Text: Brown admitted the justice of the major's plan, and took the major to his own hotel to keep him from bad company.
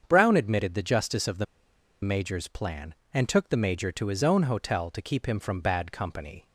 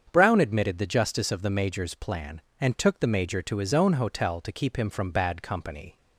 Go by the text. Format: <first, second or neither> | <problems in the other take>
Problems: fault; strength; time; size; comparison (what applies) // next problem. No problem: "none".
second | starts louder than the rest; strong; until 1.0 s; 7.5 dB; strong in the second // pauses between "the" and "major's"; noticeable; at 1.4 s; 0.58 s long